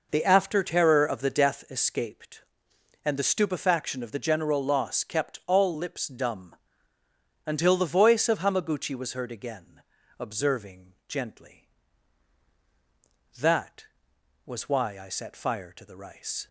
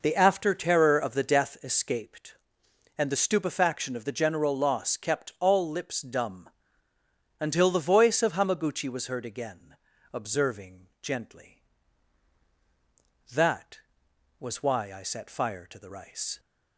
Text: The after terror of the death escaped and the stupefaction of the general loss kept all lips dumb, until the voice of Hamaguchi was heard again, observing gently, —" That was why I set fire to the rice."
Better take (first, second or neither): neither